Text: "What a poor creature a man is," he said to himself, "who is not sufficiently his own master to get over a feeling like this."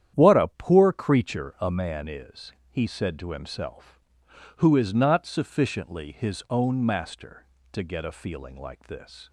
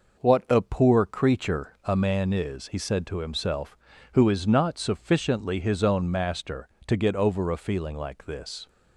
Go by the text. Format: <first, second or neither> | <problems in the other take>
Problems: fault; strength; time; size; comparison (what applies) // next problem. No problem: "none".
second | starts louder than the rest; strong; until 1.1 s; 10 dB // skips "over"; at 8.0 s